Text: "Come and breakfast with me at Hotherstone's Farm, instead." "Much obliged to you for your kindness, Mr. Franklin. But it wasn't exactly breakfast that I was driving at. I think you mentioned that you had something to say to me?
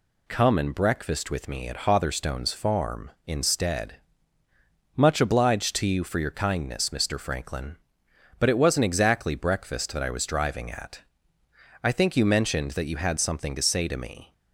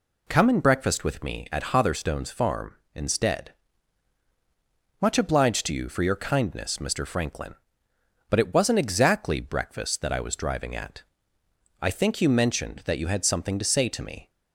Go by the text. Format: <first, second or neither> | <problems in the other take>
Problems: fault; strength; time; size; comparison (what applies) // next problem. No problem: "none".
neither | none